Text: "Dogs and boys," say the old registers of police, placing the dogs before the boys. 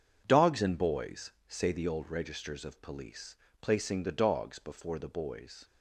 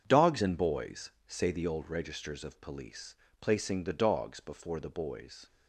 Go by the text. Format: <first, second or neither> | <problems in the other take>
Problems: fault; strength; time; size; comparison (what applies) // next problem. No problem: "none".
neither | none